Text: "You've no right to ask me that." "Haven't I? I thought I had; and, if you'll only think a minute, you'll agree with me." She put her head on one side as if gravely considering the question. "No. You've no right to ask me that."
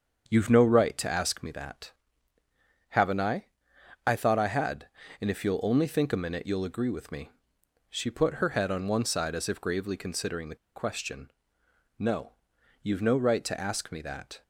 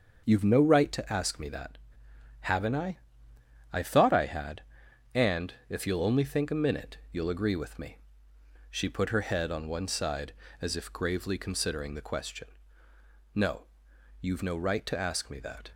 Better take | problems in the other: second | starts louder than the rest; until 1.2 s; 7 dB; noticeable in the second // pauses between "the" and "question"; slight; at 10.5 s; 0.20 s long

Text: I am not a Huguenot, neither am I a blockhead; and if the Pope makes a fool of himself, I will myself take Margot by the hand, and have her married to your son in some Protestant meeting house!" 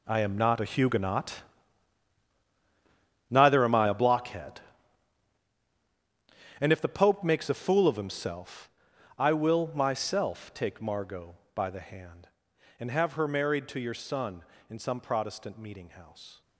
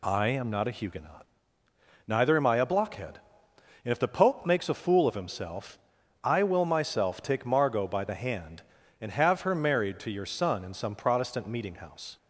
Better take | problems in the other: second | gets quieter; strong; throughout; 14 dB

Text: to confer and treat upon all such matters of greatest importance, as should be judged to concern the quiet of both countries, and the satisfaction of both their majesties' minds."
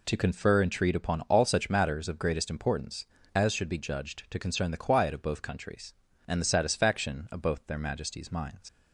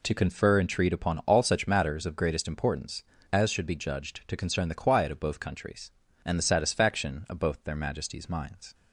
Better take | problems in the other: second | leaves "minds" unfinished; at 8.6 s; 80 ms

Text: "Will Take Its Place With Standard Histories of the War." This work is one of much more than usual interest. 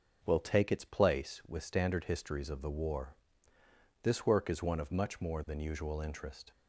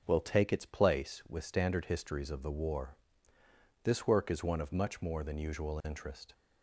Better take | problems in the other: neither | starts louder than the rest; the same in both

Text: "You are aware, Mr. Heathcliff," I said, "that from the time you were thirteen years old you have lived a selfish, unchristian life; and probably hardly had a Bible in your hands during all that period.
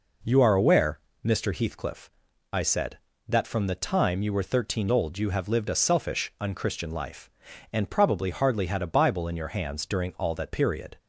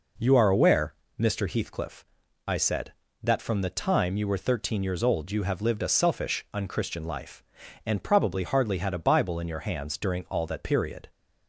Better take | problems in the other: second | skips "years"; at 4.8 s

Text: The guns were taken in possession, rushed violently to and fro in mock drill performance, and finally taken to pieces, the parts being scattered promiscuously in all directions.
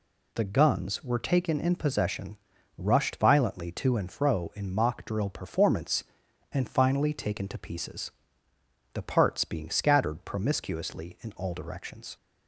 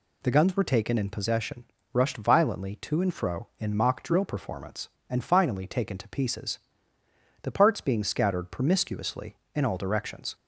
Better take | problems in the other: neither | none

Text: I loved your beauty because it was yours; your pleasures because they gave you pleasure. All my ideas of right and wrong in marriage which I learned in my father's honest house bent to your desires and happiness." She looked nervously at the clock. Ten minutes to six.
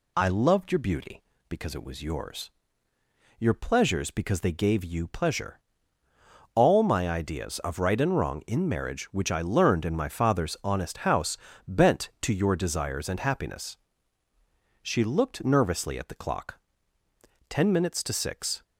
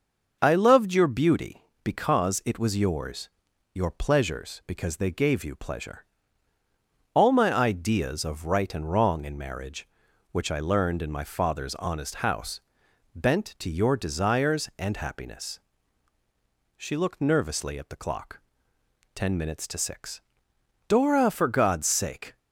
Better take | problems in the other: first | starts louder than the rest; noticeable; until 1.4 s; 6 dB // pauses between "house" and "bent"; noticeable; at 12.6 s; 0.56 s long; slight in the first // goes on to say "Dora for God's sake"; from 20.8 s on; 1.5 s long

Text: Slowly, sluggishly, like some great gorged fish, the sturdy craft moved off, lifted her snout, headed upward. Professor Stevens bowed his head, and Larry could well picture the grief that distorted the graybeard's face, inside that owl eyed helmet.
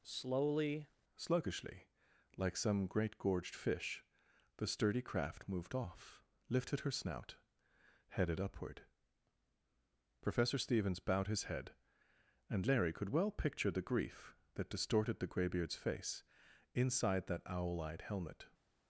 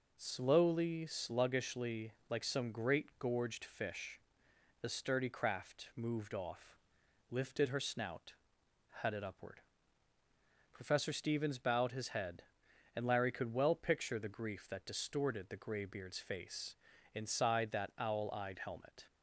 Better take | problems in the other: second | changes voice at "sluggishly"; from 1.1 s on; 17.3 s long

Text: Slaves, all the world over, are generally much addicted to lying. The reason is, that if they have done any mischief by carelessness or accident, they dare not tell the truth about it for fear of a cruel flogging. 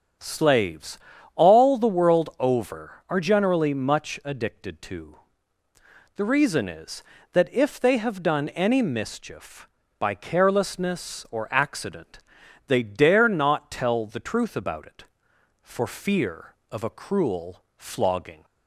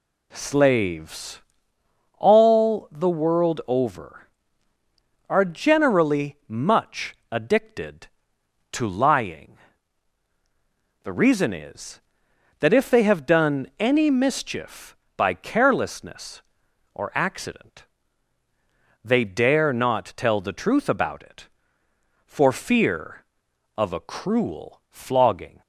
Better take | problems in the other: second | starts louder than the rest; strong; until 1.5 s; 7.5 dB // skips "lying"; at 5.6 s

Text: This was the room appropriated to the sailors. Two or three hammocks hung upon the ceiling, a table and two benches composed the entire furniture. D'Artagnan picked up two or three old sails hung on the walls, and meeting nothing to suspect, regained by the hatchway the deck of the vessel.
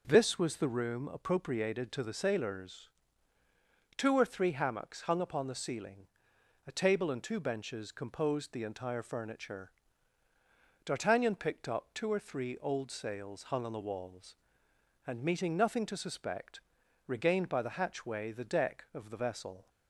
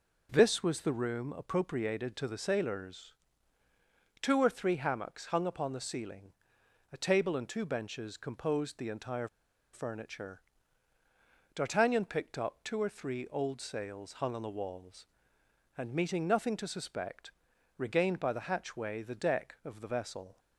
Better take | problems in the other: first | pauses between "entire" and "furniture"; noticeable; at 9.2 s; 0.46 s long

